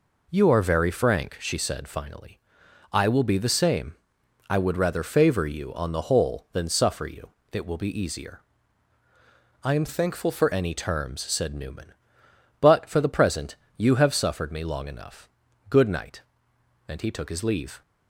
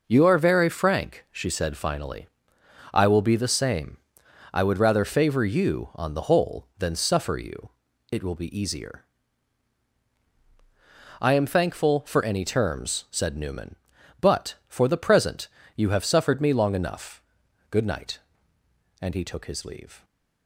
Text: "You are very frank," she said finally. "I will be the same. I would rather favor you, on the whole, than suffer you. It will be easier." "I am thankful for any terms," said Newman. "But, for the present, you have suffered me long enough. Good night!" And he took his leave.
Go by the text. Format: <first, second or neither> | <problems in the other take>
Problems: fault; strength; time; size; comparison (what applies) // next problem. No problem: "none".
second | changes voice from "thankful" to "for"; from 9.8 to 10.4 s; 0.6 s long